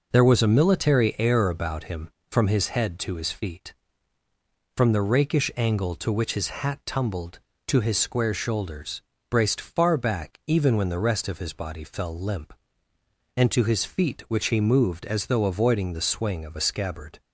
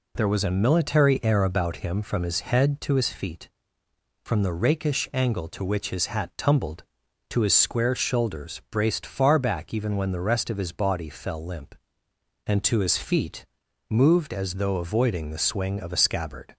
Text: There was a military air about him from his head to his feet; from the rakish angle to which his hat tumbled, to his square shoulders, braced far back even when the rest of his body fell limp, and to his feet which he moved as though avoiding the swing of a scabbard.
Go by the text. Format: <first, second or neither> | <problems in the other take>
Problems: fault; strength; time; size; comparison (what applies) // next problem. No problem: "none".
first | skips "which he"; at 13.6 s